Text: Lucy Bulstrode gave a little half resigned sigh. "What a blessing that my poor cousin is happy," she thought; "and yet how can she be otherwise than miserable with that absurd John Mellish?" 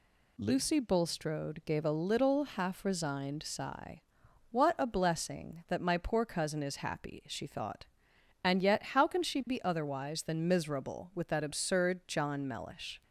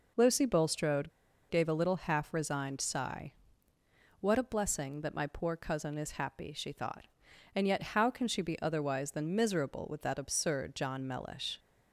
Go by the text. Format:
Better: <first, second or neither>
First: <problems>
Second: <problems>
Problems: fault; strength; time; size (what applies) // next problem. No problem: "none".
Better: first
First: none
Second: pauses between "Bulstrode" and "gave"; at 1.0 s; 0.39 s long